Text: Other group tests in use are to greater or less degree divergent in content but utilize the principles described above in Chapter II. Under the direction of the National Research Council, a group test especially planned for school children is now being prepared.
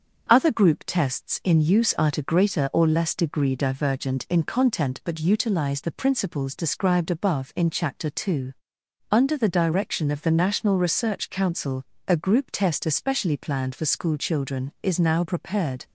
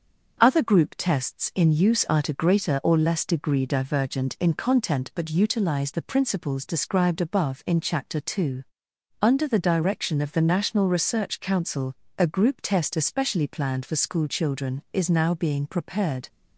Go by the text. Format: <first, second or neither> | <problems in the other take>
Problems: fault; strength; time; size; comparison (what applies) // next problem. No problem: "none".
second | starts louder than the rest; until 1.3 s; 6.5 dB; also in the second // skips "being"; at 15.2 s